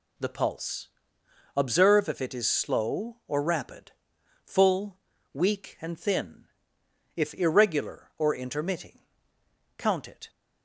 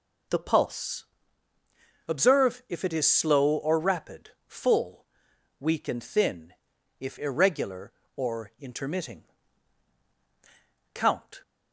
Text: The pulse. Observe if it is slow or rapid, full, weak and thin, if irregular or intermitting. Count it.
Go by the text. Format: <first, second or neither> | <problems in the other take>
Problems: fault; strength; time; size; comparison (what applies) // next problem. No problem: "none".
first | stops before "it"; at 11.4 s